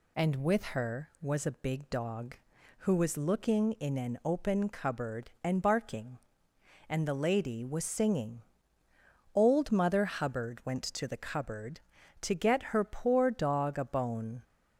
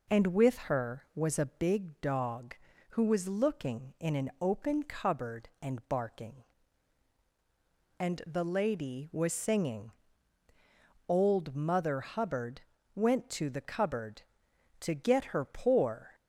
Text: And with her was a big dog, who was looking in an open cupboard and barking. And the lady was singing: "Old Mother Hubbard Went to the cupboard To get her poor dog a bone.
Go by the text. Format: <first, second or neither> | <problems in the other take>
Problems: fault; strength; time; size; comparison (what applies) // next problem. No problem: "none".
first | pauses between "Hubbard" and "Went"; slight; at 12.6 s; 0.32 s long // stops before "dog a bone"; at 16.1 s